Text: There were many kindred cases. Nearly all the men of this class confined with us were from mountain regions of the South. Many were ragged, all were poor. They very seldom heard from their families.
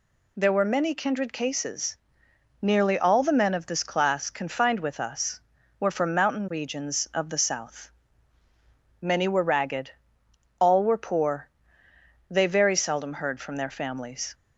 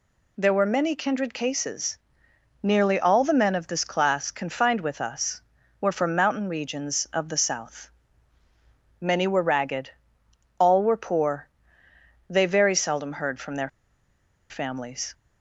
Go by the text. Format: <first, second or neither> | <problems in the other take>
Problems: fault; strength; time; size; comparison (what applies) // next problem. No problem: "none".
first | pauses between "their" and "families"; noticeable; at 13.6 s; 0.80 s long